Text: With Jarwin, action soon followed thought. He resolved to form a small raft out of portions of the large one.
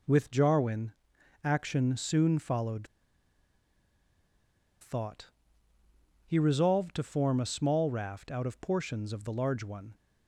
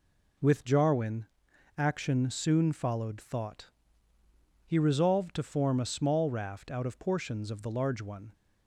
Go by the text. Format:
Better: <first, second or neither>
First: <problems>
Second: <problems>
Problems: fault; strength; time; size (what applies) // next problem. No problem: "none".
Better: second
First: pauses between "followed" and "thought"; strong; at 2.8 s; 1.9 s long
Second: none